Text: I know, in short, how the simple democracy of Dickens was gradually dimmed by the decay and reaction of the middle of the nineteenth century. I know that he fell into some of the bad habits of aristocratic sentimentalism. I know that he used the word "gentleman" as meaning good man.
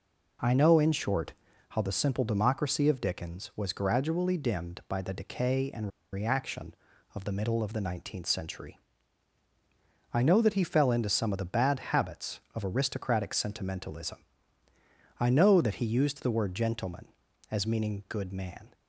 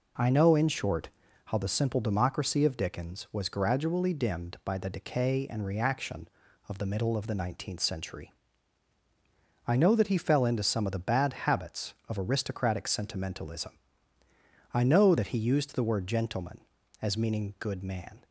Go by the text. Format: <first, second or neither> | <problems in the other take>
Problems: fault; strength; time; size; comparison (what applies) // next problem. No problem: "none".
second | pauses between "and" and "reaction"; slight; at 5.8 s; 0.24 s long